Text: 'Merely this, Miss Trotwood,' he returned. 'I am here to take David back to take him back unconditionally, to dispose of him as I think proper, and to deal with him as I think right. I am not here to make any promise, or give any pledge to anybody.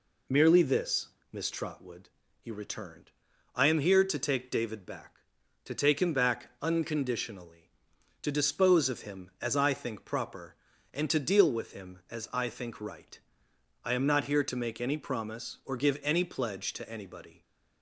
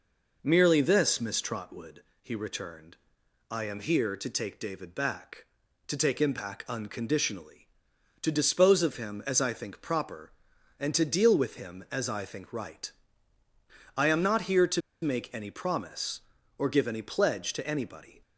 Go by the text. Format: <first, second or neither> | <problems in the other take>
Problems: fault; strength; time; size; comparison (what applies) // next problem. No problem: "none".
first | pauses between "to" and "make"; slight; at 14.8 s; 0.22 s long